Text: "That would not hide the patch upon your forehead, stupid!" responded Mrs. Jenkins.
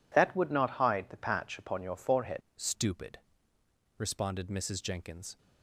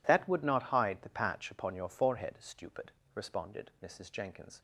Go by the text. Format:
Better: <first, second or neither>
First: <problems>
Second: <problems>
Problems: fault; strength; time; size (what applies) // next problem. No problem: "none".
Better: second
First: changes voice at "stupid"; from 2.5 s on; 2.8 s long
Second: none